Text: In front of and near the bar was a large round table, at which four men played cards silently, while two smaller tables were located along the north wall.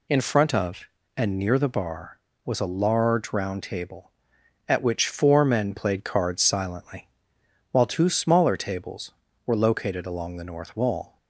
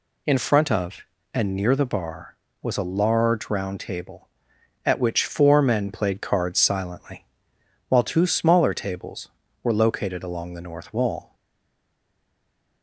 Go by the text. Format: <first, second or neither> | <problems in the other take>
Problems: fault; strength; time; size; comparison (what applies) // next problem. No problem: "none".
first | stays silent after the last word; noticeable; from 11.3 s on; 1.5 s long